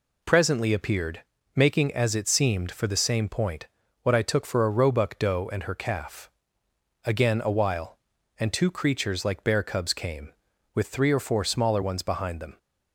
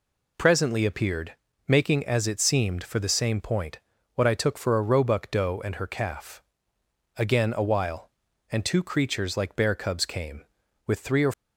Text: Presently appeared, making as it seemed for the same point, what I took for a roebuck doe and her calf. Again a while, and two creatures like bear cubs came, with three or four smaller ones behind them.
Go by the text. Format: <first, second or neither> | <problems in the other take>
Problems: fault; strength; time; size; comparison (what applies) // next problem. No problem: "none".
first | stops before "four smaller ones behind them"; at 11.3 s